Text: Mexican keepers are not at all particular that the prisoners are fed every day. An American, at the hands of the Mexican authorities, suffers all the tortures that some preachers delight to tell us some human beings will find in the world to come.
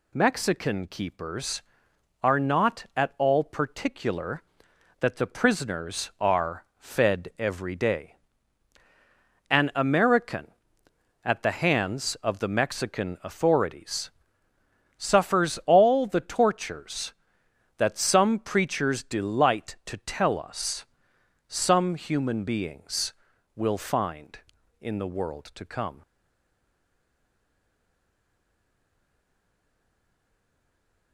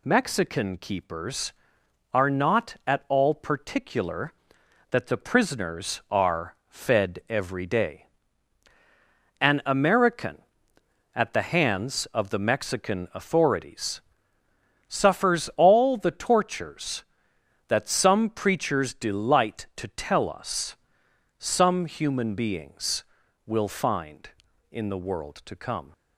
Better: second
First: pauses between "us" and "some"; noticeable; at 20.8 s; 0.62 s long // stays silent after the last word; strong; from 26.0 s on; 5.1 s long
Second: pauses between "us" and "some"; noticeable; at 20.7 s; 0.62 s long

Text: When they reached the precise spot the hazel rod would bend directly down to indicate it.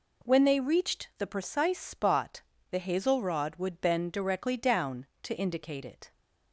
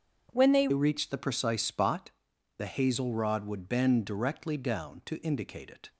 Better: first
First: pauses between "spot" and "the"; slight; at 2.4 s; 0.28 s long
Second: changes voice at "reached"; from 0.7 s on; 5.2 s long // pauses between "spot" and "the"; noticeable; at 2.1 s; 0.46 s long

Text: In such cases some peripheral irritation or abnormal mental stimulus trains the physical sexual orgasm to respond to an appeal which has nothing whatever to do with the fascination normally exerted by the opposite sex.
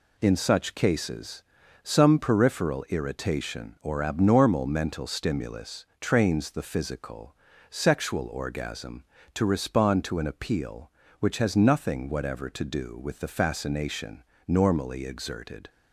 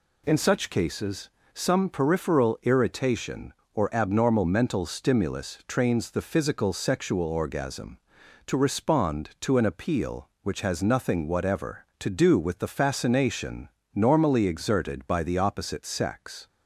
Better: second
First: pauses between "cases" and "some"; at 1.4 s; 0.40 s long // pauses between "stimulus" and "trains"; slight; at 5.8 s; 0.16 s long // pauses between "physical" and "sexual"; slight; at 7.3 s; 0.34 s long // pauses between "fascination" and "normally"; slight; at 14.2 s; 0.24 s long // stops before "by the opposite sex"; at 15.6 s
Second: pauses between "cases" and "some"; slight; at 1.2 s; 0.24 s long // pauses between "fascination" and "normally"; slight; at 13.6 s; 0.24 s long

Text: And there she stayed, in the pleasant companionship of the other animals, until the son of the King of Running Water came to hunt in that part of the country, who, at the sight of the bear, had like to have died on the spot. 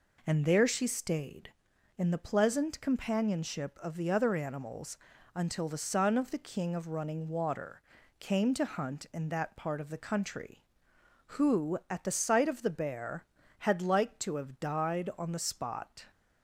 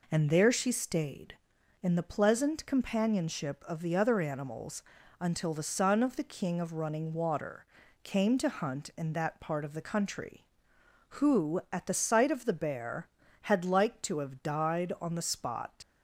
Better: first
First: pauses between "Water" and "came"; at 7.8 s; 0.38 s long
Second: pauses between "Water" and "came"; at 7.6 s; 0.38 s long // leaves "spot" unfinished; at 15.8 s; 105 ms

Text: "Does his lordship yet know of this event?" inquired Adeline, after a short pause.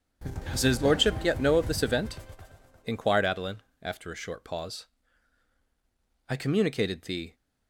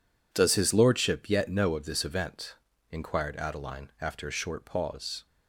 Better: second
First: goes on to say "I communicated the"; noticeable; from 6.2 s on; 1.0 s long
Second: none

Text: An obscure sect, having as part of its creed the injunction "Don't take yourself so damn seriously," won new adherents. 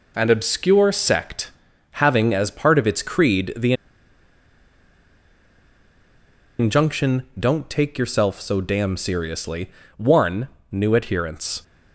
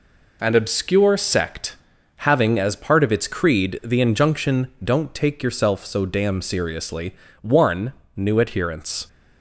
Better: second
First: pauses between "the" and "injunction"; strong; at 3.7 s; 2.8 s long // pauses between "injunction" and "Don't"; slight; at 7.2 s; 0.16 s long // pauses between "won" and "new"; slight; at 10.4 s; 0.20 s long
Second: pauses between "injunction" and "Don't"; slight; at 4.6 s; 0.16 s long // pauses between "won" and "new"; slight; at 7.9 s; 0.20 s long

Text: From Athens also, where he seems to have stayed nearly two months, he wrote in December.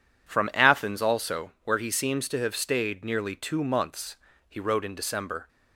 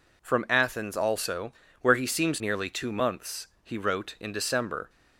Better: first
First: none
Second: skips "to have stayed"; at 2.4 s

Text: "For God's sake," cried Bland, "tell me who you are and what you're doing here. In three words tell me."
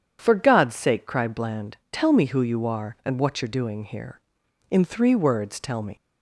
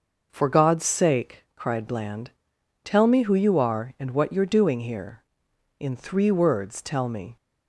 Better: second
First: starts louder than the rest; strong; until 1.2 s; 8.5 dB // leaves "me" unfinished; at 5.9 s; 130 ms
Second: none

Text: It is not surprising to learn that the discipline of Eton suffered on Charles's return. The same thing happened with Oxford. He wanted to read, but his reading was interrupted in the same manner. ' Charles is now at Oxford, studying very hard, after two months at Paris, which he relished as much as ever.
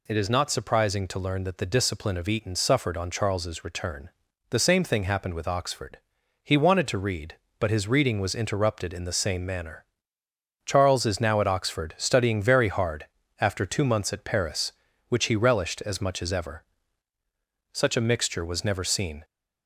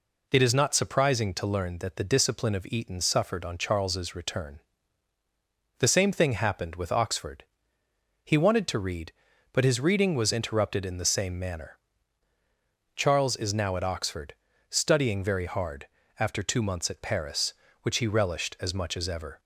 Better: second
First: goes on to say "Such a mixture was never seen"; from 17.7 s on; 1.5 s long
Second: none

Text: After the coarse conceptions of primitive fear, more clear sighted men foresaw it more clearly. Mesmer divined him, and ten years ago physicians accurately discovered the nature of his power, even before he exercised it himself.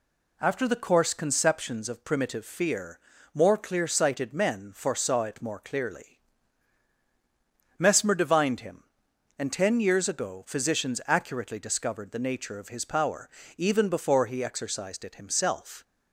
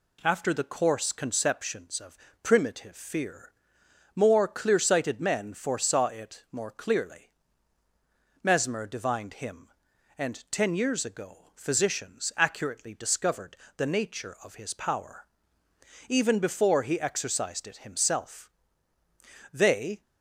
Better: first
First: none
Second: pauses between "of" and "primitive"; slight; at 2.1 s; 0.26 s long // pauses between "discovered" and "the"; slight; at 13.5 s; 0.22 s long // goes on to say "They"; slight; from 19.5 s on; 0.48 s long

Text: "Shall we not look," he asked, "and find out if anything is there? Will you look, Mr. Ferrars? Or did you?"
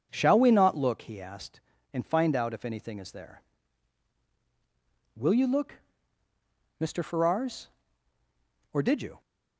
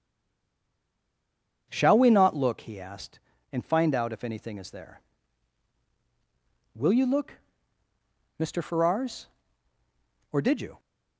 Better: first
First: none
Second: stays silent before the first word; noticeable; until 1.6 s; 1.6 s long

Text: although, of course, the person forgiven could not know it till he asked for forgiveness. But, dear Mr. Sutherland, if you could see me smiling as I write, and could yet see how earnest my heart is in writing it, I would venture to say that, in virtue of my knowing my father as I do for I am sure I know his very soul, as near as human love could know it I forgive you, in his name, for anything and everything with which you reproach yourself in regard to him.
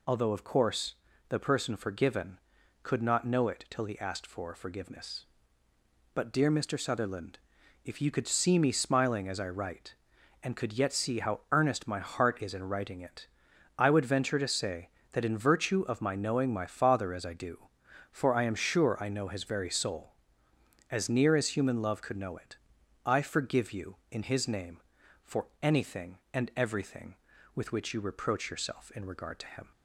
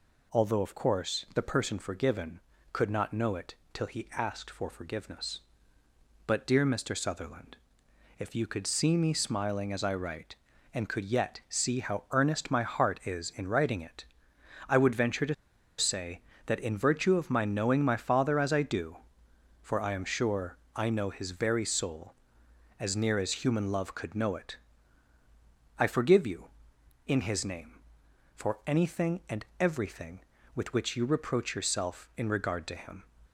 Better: first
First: pauses between "it" and "I"; noticeable; at 22.5 s; 0.48 s long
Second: pauses between "it" and "till"; slight; at 3.5 s; 0.18 s long // pauses between "to" and "say"; at 15.3 s; 0.43 s long // pauses between "sure" and "I"; slight; at 20.5 s; 0.18 s long // pauses between "it" and "I"; at 24.5 s; 1.2 s long // pauses between "and" and "everything"; slight; at 29.4 s; 0.16 s long

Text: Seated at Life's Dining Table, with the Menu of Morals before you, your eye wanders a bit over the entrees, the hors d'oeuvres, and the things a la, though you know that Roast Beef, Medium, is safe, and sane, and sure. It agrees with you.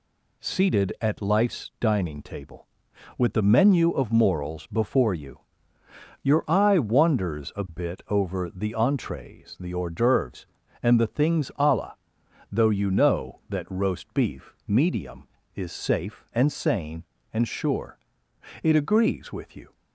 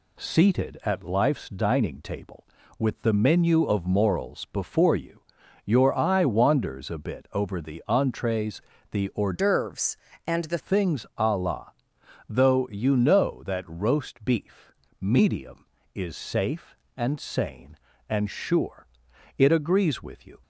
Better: first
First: none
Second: changes voice from "d'oeuvres" to "the"; from 9.3 to 10.5 s; 1.2 s long

